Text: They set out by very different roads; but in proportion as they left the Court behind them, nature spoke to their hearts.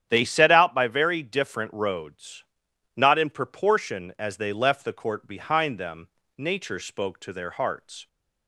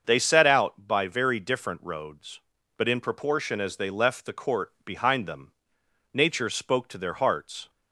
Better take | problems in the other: second | starts louder than the rest; strong; until 1.1 s; 9.5 dB; also in the second // says "not" for "but"; at 2.9 s

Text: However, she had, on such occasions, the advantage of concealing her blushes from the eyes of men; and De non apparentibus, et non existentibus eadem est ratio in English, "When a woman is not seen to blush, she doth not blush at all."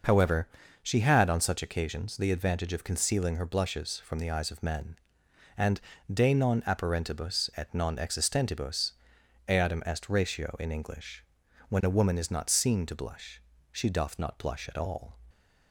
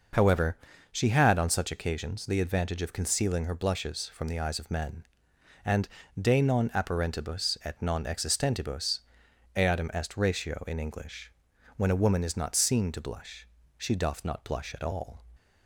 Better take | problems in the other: neither | pauses between "and" and "De"; slight; the same in both // pauses between "existentibus" and "eadem"; noticeable; the same in both

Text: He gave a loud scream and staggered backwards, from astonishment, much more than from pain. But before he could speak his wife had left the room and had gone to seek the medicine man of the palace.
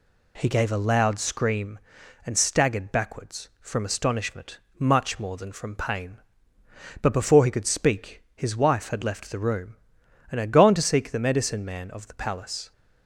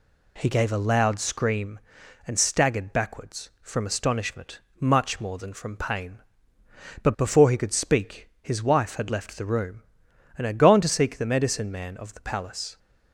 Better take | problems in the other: neither | none

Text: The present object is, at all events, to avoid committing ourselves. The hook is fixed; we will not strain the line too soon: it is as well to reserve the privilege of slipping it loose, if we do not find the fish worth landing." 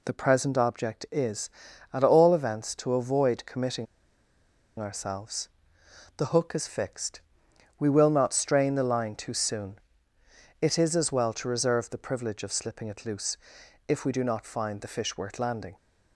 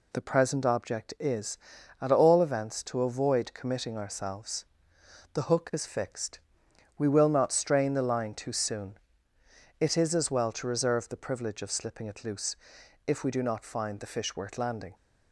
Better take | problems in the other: second | pauses between "committing" and "ourselves"; noticeable; at 3.8 s; 0.94 s long

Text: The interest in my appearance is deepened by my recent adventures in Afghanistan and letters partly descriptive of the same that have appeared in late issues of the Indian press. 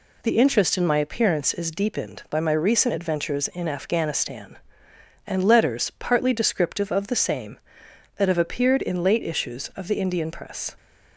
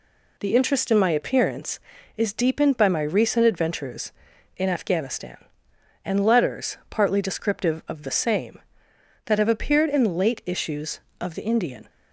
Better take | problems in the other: first | stops before "press"; at 11.8 s

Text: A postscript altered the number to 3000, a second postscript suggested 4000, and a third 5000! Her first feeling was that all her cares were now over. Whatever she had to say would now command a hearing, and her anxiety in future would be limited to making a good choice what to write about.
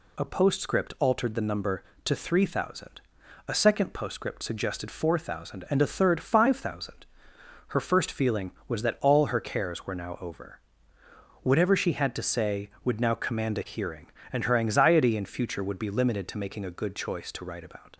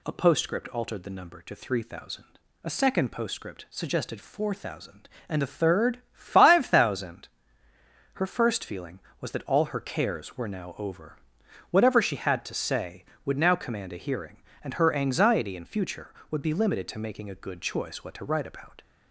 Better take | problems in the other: second | skips "what"; at 17.3 s

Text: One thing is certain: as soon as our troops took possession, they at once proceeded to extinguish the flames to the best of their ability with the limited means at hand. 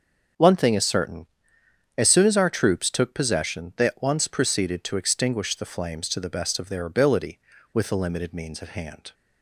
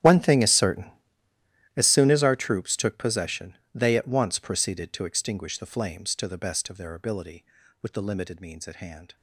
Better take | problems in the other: first | gets quieter; strong; throughout; 20 dB // starts louder than the rest; strong; until 1.8 s; 11 dB; also in the first

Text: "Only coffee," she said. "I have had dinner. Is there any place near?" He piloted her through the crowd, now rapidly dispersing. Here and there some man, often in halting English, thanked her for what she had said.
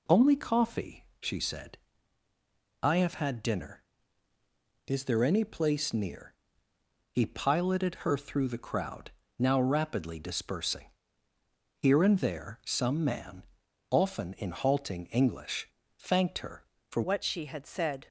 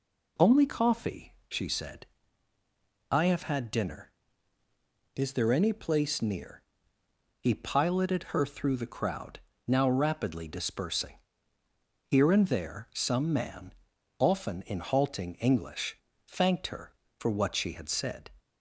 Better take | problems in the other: second | changes voice at "what"; from 17.0 s on; 1.0 s long

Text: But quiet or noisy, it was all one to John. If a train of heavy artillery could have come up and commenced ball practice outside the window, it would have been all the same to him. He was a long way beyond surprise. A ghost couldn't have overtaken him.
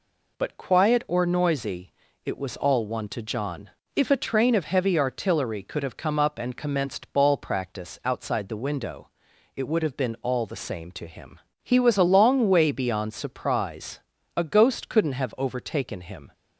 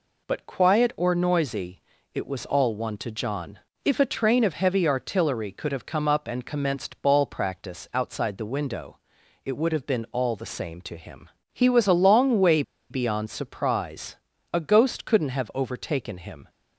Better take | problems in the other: first | pauses between "way" and "beyond"; slight; at 12.6 s; 0.28 s long

